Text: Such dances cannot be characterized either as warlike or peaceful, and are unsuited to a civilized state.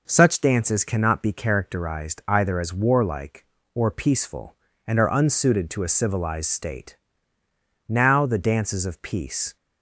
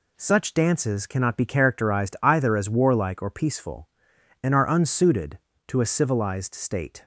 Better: second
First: goes on to say "Now the dances of peace"; strong; from 7.8 s on; 1.6 s long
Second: none

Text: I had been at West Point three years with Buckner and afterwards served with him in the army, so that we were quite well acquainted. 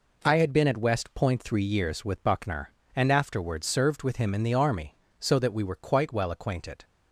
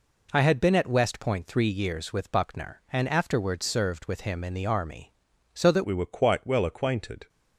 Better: first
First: none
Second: changes voice at "we"; from 5.8 s on; 1.4 s long

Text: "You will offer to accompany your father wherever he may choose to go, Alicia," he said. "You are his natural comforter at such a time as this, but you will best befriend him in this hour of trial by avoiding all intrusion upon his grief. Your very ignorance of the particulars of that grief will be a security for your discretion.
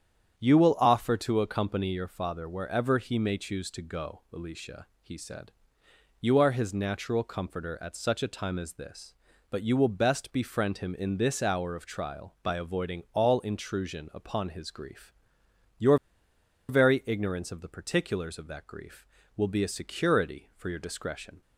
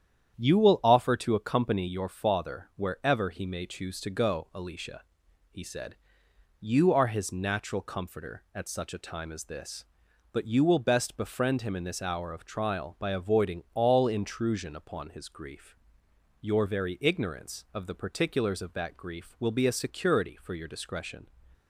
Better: second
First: starts louder than the rest; strong; until 1.4 s; 9 dB // pauses between "Your" and "very"; noticeable; at 15.9 s; 0.72 s long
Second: starts louder than the rest; strong; until 1.3 s; 9.5 dB

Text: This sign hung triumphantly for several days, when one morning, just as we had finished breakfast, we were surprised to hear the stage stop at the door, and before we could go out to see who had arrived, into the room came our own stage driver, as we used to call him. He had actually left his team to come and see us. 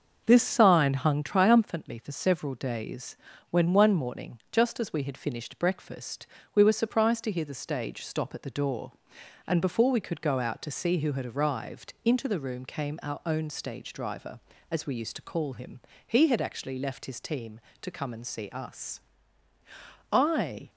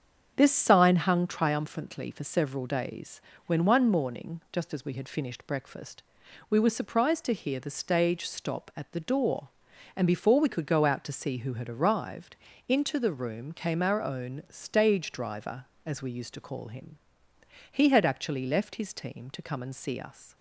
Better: second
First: starts louder than the rest; until 1.2 s; 6.5 dB // goes on to say "I"; from 20.0 s on; 0.60 s long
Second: starts louder than the rest; strong; until 1.3 s; 7.5 dB

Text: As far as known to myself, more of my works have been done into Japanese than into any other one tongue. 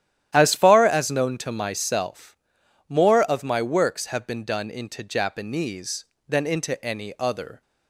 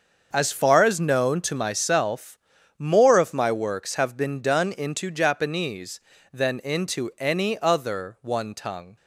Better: second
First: starts louder than the rest; strong; until 1.3 s; 11.5 dB // stops before "one tongue"; at 7.6 s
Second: starts louder than the rest; until 1.3 s; 6.5 dB

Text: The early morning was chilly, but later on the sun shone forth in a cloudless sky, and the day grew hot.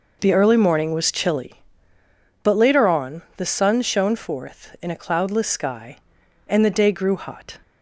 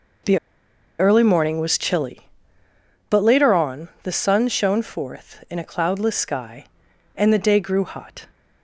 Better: first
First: pauses between "on" and "the"; slight; at 3.2 s; 0.16 s long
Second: pauses between "The" and "early"; noticeable; at 0.3 s; 0.61 s long // pauses between "on" and "the"; slight; at 3.8 s; 0.16 s long

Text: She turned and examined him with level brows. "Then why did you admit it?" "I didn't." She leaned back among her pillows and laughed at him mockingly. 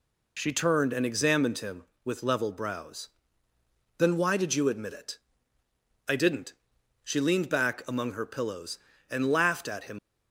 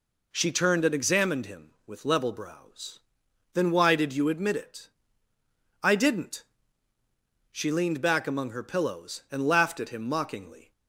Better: second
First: stops before "mockingly"; at 9.9 s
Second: none

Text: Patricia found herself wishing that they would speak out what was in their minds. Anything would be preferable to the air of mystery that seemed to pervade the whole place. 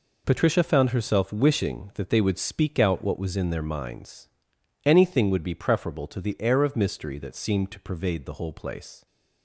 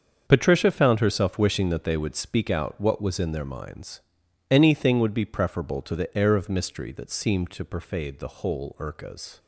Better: first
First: none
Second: starts louder than the rest; until 1.2 s; 7 dB // says "urcas" for "place"; at 8.7 s

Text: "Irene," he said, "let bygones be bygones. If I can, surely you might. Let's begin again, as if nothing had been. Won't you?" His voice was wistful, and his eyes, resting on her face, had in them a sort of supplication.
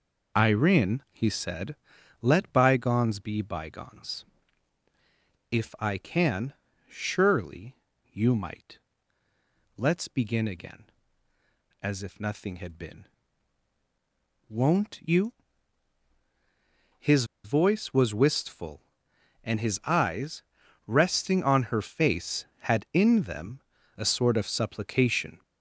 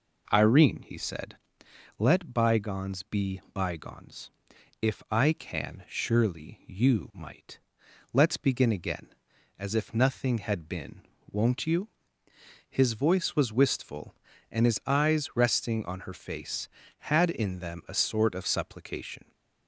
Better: second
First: pauses between "surely" and "you"; at 7.7 s; 0.38 s long // pauses between "His" and "voice"; slight; at 17.2 s; 0.19 s long // pauses between "them" and "a"; at 23.5 s; 0.38 s long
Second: none

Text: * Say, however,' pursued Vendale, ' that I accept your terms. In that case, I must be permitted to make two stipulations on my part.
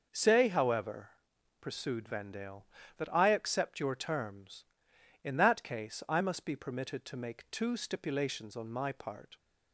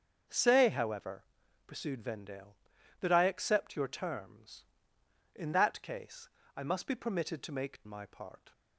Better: first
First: none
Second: starts louder than the rest; until 1.7 s; 7 dB // skips "two stipulations on"; at 7.8 s

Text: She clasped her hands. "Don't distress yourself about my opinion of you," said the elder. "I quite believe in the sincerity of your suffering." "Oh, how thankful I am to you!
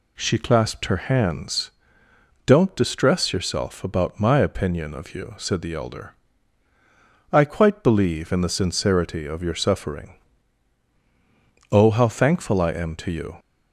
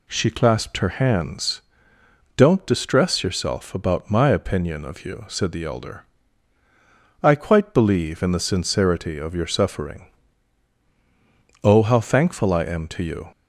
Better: neither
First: none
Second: none

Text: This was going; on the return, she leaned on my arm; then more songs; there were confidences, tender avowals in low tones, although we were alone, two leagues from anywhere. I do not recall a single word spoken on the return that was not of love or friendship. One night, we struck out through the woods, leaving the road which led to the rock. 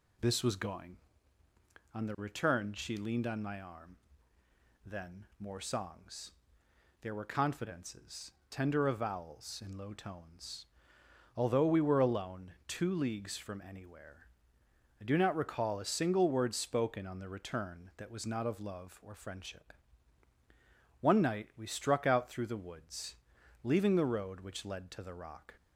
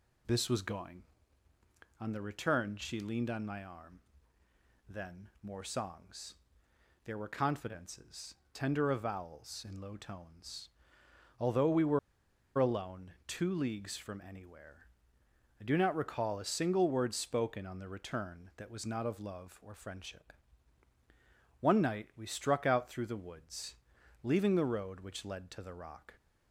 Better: first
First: none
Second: pauses between "were" and "alone"; noticeable; at 11.9 s; 0.59 s long

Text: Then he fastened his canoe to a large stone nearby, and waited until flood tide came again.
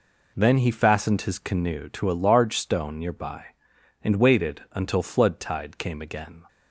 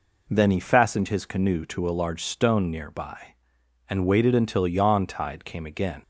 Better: first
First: none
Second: says "yawn" for "flood"; at 4.6 s

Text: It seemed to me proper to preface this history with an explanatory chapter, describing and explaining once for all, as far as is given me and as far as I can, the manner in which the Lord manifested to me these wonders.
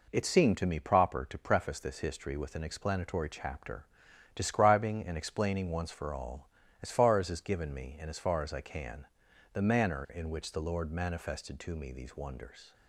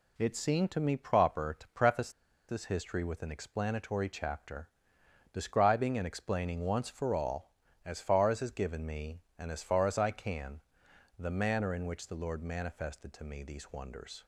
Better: first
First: none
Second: pauses between "preface" and "this"; at 2.0 s; 0.39 s long

